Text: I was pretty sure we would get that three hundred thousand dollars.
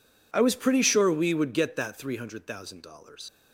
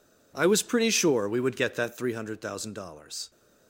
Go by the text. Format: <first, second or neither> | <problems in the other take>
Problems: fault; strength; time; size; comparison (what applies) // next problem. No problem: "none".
second | leaves "dollars" unfinished; at 3.2 s; 135 ms